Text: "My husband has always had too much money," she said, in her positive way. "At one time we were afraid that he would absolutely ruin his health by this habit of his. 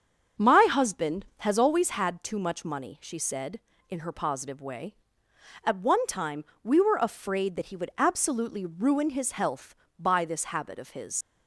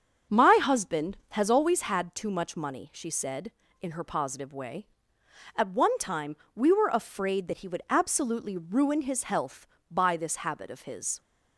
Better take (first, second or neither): second